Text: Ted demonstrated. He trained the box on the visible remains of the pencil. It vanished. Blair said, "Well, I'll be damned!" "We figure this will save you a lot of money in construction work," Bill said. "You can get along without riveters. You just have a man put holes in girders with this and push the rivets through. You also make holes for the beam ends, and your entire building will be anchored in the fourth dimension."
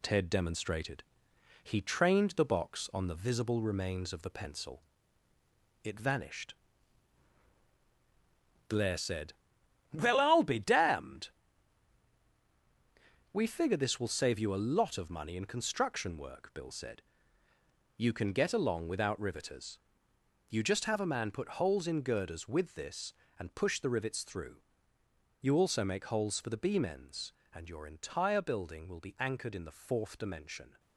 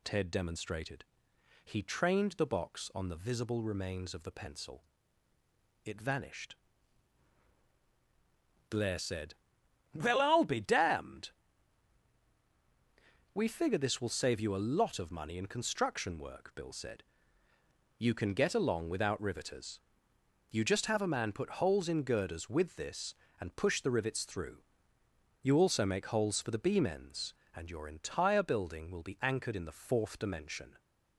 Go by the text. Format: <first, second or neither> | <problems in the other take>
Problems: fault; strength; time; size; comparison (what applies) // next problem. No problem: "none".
second | gets quieter; noticeable; throughout; 5.5 dB